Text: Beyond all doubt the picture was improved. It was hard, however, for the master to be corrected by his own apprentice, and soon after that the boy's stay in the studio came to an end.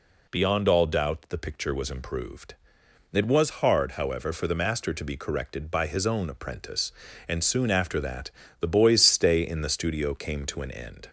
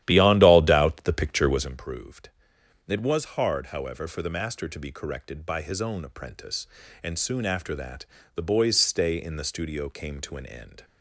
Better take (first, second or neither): first